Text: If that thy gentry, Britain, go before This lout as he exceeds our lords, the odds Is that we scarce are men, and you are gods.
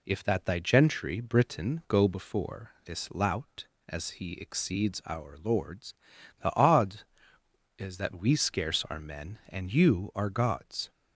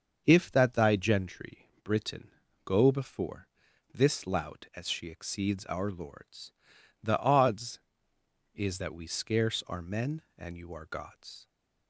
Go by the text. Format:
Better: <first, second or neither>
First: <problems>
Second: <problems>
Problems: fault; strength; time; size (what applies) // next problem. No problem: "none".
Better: first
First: none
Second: starts louder than the rest; until 1.2 s; 6.5 dB // pauses between "before" and "This"; noticeable; at 3.4 s; 0.46 s long // says "she" for "he"; at 4.8 s